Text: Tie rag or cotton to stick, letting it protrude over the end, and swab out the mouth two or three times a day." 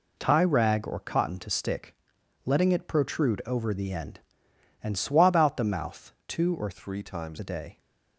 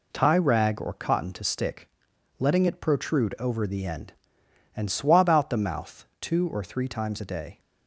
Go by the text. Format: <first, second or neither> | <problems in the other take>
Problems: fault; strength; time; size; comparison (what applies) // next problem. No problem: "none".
second | changes voice from "three" to "times"; from 6.7 to 7.3 s; 0.6 s long